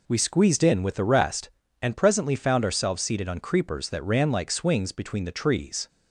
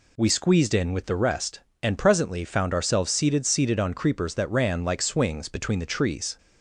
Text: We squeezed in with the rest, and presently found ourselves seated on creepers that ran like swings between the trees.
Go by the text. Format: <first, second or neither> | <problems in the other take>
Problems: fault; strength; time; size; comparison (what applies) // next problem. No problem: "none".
first | says "seated" twice; at 3.4 s